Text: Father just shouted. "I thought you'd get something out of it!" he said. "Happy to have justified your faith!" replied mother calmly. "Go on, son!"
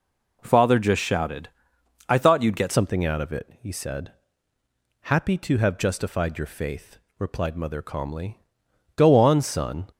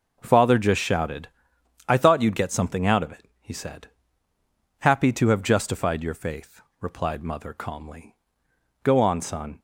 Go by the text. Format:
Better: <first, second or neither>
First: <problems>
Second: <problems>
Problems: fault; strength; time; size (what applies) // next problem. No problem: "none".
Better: second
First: changes voice at "something"; from 2.7 s on; 7.1 s long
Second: none